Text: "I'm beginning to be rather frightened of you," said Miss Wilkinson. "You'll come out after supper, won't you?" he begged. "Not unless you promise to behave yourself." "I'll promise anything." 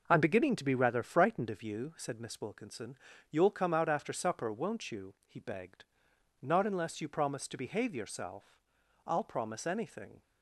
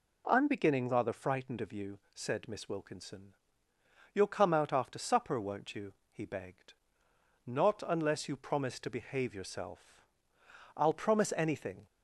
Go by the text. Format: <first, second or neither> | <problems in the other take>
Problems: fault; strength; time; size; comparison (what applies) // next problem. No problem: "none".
first | skips "to be"; at 0.8 s